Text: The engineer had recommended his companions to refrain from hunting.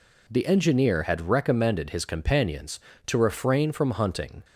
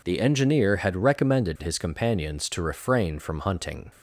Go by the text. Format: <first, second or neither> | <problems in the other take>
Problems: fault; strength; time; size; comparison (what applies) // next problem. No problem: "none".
neither | none